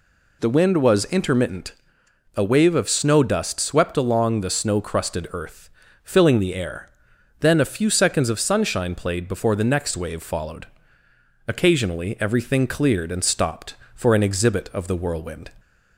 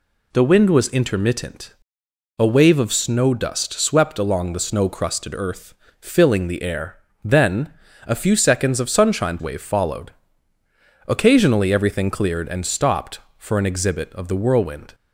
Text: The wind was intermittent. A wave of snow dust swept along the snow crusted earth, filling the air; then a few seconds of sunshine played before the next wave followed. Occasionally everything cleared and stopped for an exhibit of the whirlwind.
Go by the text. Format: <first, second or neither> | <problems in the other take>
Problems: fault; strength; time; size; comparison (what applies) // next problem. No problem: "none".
first | pauses between "then" and "a"; slight; at 7.7 s; 0.34 s long // skips "played before the next"; at 9.3 s